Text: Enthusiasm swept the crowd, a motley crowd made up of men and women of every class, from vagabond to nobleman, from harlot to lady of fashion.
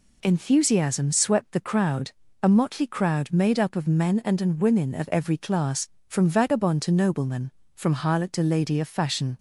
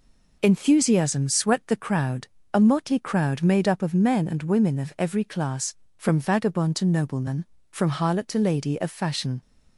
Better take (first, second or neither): second